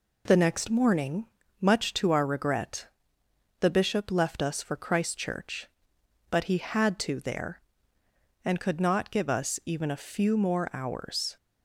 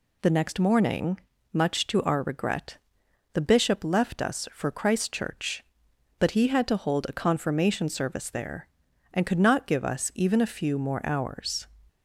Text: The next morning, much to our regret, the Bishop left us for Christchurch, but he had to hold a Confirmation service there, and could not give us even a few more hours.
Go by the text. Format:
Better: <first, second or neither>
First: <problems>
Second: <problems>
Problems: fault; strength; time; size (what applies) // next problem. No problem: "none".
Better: second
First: skips "hold a Confirmation service"; at 7.2 s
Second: none